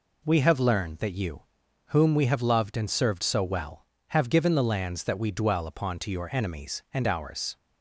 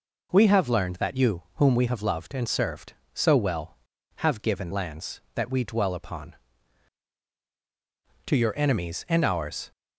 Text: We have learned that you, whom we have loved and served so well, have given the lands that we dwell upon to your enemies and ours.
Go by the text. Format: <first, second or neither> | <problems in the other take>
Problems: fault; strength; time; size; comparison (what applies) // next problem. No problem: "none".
first | skips "the"; at 4.7 s